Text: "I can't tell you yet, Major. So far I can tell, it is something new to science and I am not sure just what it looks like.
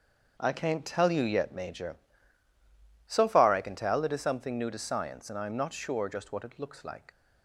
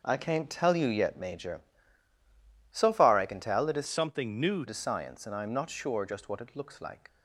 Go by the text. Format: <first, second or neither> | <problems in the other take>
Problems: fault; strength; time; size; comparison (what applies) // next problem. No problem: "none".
first | starts louder than the rest; until 1.0 s; 6.5 dB; also in the first // changes voice from "something" to "new"; from 3.8 to 4.6 s; 0.8 s long